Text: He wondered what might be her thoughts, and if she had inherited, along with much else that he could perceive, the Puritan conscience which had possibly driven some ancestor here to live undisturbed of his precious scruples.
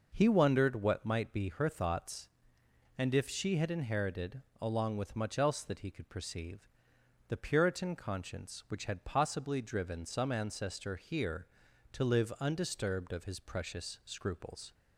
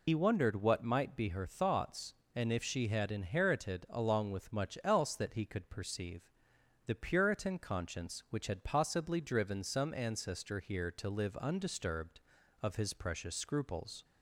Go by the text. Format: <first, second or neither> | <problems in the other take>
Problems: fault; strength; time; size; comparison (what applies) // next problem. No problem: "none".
first | loses the start of "He"; at 0.0 s; 70 ms